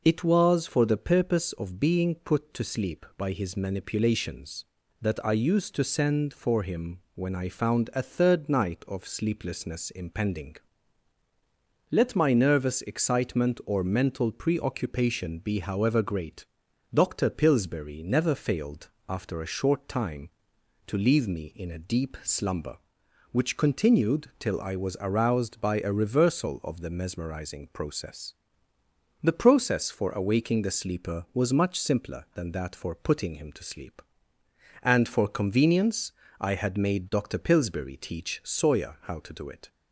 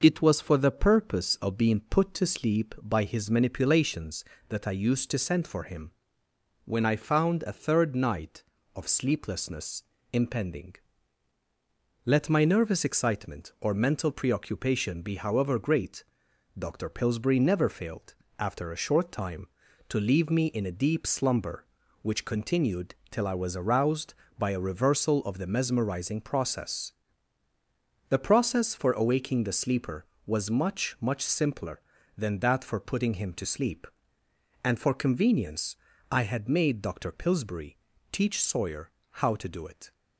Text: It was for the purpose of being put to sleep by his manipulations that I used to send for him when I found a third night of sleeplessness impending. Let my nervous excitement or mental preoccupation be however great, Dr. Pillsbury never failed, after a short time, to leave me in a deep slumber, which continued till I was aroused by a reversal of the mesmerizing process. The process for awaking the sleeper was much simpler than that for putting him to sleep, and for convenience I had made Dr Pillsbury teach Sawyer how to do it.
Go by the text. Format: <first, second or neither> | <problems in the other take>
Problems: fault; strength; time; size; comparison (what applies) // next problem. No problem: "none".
first | pauses between "him" and "when"; noticeable; at 5.9 s; 0.72 s long; slight in the first // pauses between "sleeplessness" and "impending"; slight; at 9.8 s; 0.28 s long // pauses between "continued" and "till"; slight; at 22.9 s; 0.16 s long // says "much" twice; at 31.0 s // pauses between "convenience" and "I"; slight; at 35.7 s; 0.34 s long; slight in the first // pauses between "Pillsbury" and "teach"; slight; at 37.7 s; 0.32 s long // pauses between "Sawyer" and "how"; slight; at 38.8 s; 0.32 s long